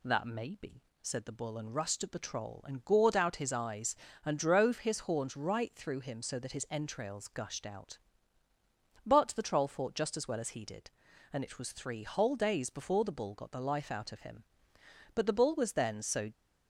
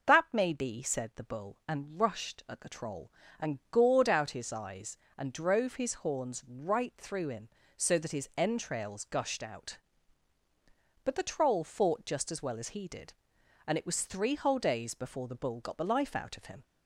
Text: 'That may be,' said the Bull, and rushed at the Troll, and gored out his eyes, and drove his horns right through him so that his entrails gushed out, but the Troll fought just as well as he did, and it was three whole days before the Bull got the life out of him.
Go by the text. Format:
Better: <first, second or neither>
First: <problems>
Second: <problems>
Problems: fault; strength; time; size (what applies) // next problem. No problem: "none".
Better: second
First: goes on to say "But the Bull was then so"; noticeable; from 15.1 s on; 1.1 s long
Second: none